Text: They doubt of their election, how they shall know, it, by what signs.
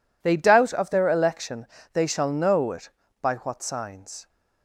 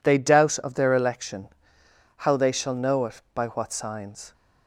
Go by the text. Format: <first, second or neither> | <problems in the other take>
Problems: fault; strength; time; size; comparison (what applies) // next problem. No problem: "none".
second | skips "how"; at 1.7 s